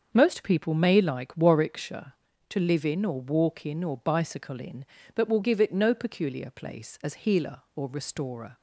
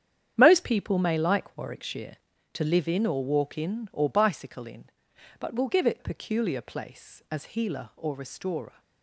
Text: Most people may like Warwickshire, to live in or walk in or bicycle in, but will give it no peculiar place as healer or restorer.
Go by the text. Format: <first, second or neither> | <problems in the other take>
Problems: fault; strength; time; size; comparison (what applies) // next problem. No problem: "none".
first | starts louder than the rest; strong; until 1.3 s; 9 dB; also in the first // skips "no"; at 5.9 s